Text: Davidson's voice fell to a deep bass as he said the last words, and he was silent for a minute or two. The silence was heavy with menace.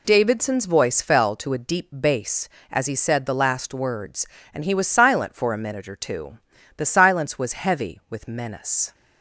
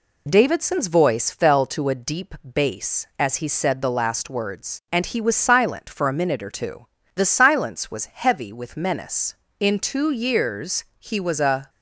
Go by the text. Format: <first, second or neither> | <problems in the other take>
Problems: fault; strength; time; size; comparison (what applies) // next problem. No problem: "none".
first | goes on to say "In two years he was a"; strong; from 9.5 s on; 2.1 s long